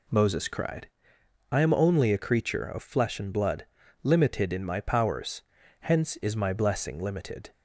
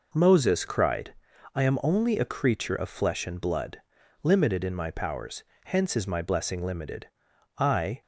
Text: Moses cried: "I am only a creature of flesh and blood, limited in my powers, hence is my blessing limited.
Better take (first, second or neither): first